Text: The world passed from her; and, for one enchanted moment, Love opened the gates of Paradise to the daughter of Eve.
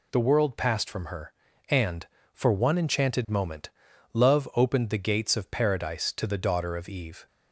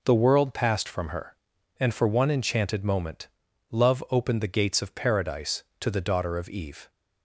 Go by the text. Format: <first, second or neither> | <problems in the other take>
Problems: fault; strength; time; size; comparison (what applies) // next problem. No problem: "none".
neither | none